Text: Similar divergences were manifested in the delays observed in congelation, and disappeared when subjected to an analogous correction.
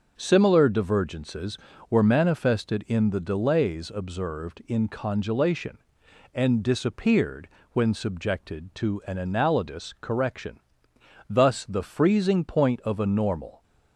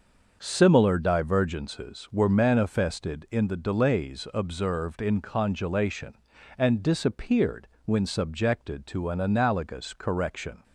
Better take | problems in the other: second | starts louder than the rest; until 1.1 s; 6 dB; also in the second // pauses between "disappeared" and "when"; slight; at 7.4 s; 0.24 s long; slight in the second // goes on to say "Thus the freezing point of a normal"; strong; from 11.2 s on; 2.3 s long

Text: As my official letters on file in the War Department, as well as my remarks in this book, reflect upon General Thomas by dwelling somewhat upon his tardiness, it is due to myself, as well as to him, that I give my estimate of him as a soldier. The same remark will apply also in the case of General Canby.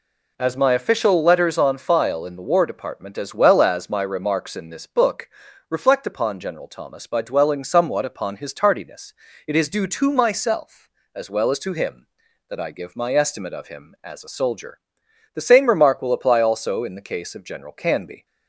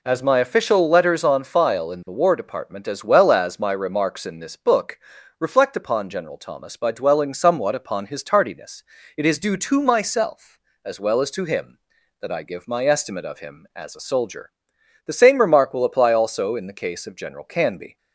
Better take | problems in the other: neither | none

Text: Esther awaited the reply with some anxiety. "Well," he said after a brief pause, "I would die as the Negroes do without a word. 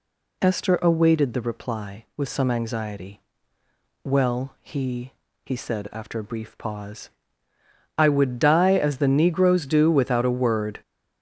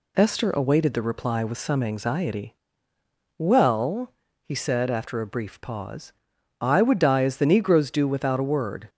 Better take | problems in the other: second | says "he" twice; at 5.4 s

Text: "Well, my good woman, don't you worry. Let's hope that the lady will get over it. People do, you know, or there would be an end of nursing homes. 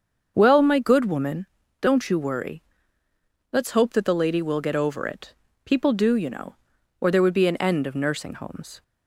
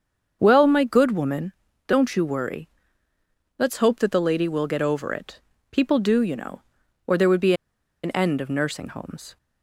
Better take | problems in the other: first | starts louder than the rest; until 1.4 s; 7 dB; also in the first // pauses between "be" and "an"; noticeable; at 7.5 s; 0.50 s long

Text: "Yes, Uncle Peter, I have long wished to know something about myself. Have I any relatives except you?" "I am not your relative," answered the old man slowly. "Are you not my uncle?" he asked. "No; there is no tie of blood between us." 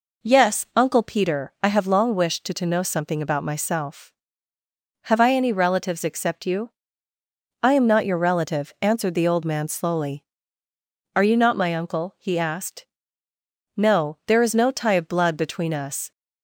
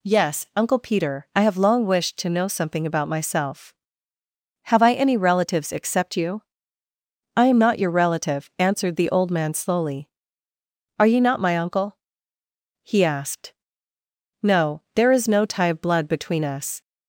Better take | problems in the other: second | says "to" twice; at 2.5 s

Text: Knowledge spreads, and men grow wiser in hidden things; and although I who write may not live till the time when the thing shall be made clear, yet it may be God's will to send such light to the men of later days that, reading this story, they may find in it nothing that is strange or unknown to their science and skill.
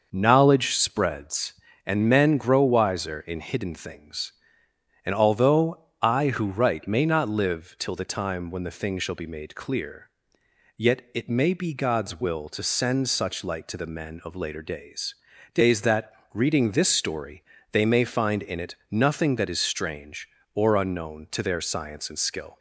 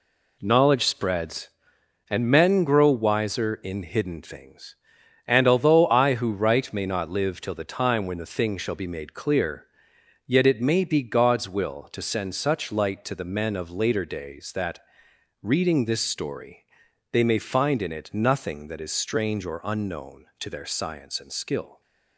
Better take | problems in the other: second | pauses between "although" and "I"; slight; at 5.7 s; 0.20 s long // says "days" twice; at 15.5 s

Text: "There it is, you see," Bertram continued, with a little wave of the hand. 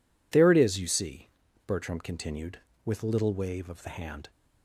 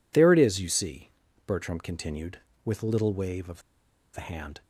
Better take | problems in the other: first | pauses between "of" and "the"; noticeable; at 3.6 s; 0.54 s long

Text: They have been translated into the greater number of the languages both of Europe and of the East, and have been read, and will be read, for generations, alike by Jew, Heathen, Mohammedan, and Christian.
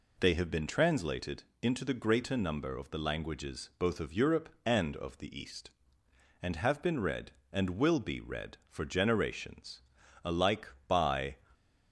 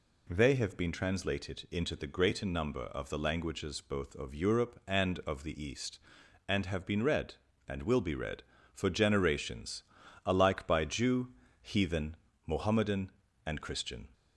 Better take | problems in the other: second | pauses between "translated" and "into"; slight; at 1.4 s; 0.18 s long // stops before "Jew Heathen Mohammedan and Christian"; at 11.5 s

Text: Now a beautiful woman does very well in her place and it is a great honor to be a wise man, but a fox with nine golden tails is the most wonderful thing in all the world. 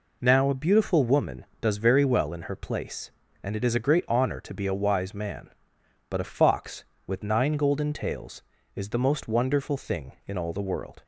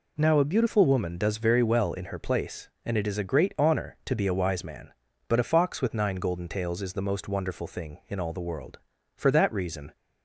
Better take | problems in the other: first | goes on to say "For that reason"; noticeable; from 9.1 s on; 0.80 s long

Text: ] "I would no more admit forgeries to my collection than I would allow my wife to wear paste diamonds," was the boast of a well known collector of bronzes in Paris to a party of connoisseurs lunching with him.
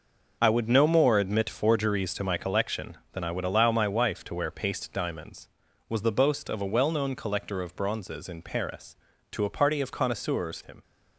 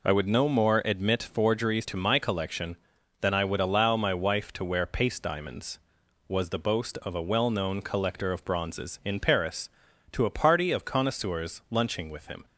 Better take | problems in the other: second | skips "lunching with"; at 10.6 s

